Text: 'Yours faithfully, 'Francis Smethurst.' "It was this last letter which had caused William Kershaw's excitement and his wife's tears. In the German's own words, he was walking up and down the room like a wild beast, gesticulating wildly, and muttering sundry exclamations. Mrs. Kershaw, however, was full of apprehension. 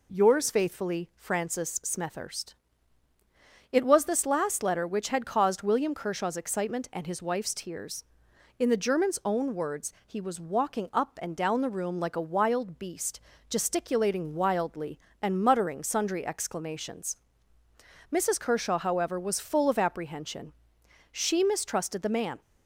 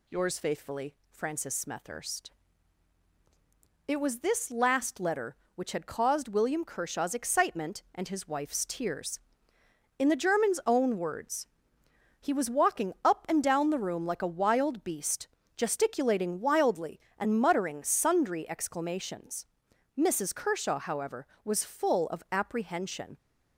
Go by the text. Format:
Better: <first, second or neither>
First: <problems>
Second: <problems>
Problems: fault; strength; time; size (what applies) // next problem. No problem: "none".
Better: second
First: goes on to say "She mistrusted the man"; noticeable; from 21.1 s on; 1.3 s long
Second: none